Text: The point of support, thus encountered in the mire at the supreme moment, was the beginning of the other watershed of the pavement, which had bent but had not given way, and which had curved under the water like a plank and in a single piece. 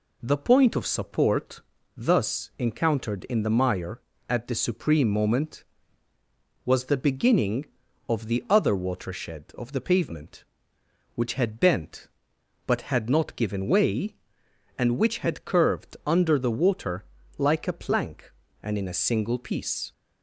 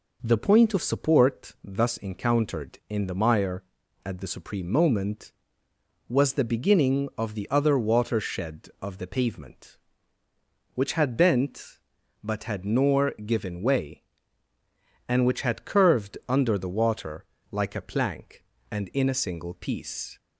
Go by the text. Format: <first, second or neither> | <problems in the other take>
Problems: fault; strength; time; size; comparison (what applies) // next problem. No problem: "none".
first | says "nor" for "not"; at 12.6 s // pauses between "water" and "like"; slight; at 17.2 s; 0.26 s long; slight in the first